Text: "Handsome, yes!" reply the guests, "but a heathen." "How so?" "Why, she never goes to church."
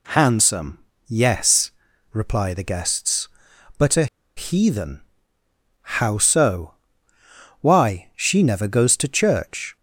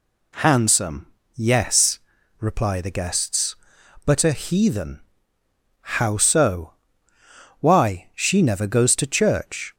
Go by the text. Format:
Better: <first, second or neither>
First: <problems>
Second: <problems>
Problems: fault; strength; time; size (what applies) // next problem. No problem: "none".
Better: second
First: pauses between "a" and "heathen"; slight; at 4.0 s; 0.30 s long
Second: none